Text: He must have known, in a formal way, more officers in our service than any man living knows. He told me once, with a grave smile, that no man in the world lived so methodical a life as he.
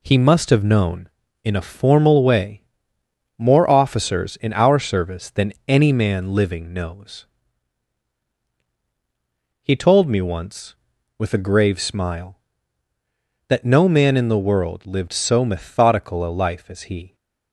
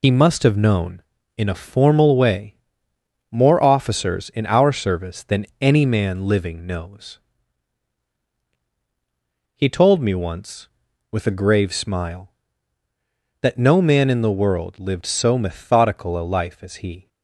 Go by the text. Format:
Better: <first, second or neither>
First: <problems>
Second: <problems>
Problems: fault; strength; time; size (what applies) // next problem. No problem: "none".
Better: first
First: none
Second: loses the start of "He"; at 0.0 s; 70 ms